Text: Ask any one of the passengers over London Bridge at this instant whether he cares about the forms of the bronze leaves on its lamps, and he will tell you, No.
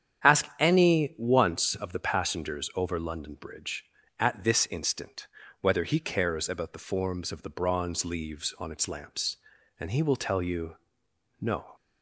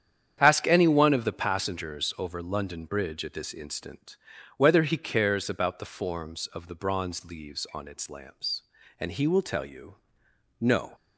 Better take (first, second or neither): second